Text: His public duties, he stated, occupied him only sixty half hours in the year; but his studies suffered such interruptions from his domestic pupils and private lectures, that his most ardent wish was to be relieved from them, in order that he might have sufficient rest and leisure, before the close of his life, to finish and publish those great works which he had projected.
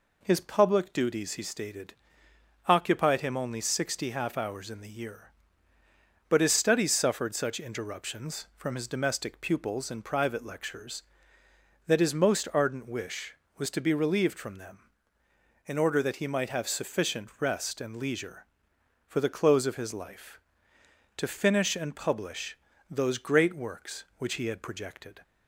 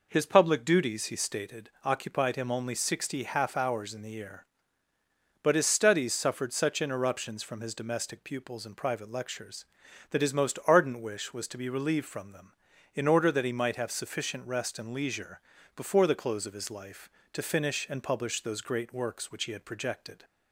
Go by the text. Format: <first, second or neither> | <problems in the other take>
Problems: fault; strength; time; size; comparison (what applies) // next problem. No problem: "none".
second | says "for" for "before"; at 19.0 s // pauses between "publish" and "those"; slight; at 22.5 s; 0.32 s long